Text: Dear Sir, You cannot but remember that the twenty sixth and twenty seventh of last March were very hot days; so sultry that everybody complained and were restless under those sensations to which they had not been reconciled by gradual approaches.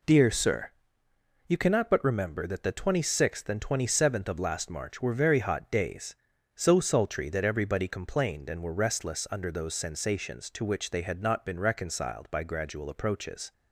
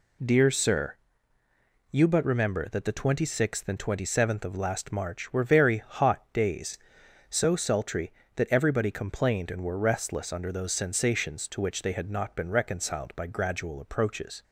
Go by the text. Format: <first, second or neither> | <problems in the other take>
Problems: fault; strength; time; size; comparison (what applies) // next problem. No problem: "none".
first | skips "cannot"; at 2.0 s